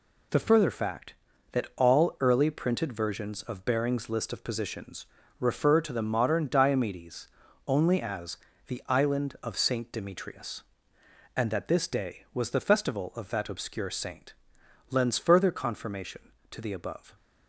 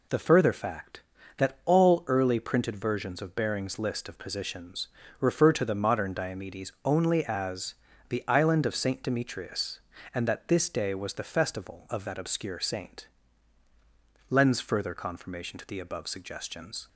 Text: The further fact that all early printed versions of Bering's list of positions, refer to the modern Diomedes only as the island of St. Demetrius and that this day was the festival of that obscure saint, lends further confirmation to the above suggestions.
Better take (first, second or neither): second